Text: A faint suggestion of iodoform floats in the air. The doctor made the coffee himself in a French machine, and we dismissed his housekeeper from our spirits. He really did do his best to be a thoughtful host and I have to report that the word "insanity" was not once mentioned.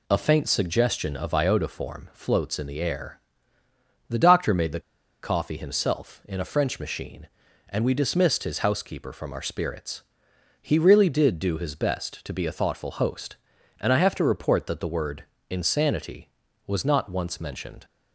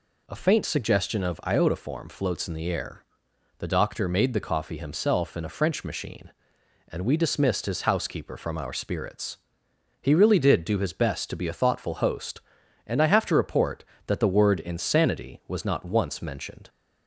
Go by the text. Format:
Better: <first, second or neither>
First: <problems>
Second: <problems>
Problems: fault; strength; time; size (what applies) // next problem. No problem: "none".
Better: second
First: pauses between "the" and "coffee"; at 4.7 s; 0.43 s long // pauses between "word" and "insanity"; slight; at 15.2 s; 0.26 s long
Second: none